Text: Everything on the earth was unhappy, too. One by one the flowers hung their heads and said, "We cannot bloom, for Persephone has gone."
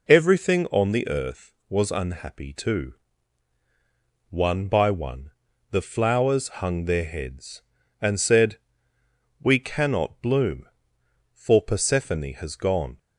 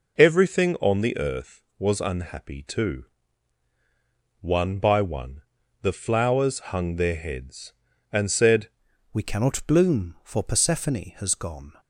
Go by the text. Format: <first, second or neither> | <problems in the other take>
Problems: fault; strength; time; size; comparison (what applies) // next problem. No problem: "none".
first | pauses between "one" and "the"; at 5.4 s; 0.40 s long; also in the first // changes voice at "We"; from 9.1 s on; 2.6 s long